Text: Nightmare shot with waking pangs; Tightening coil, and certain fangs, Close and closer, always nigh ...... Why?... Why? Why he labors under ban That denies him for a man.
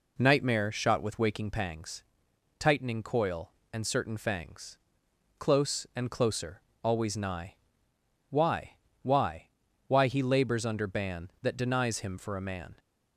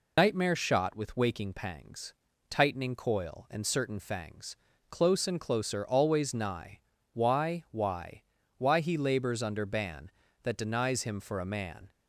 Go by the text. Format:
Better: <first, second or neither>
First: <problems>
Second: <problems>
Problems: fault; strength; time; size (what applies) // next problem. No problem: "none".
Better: first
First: none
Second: loses the start of "Nightmare"; at 0.1 s; 90 ms